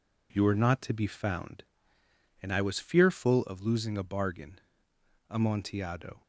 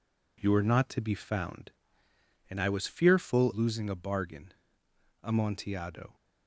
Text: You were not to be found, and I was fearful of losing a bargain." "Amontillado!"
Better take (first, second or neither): first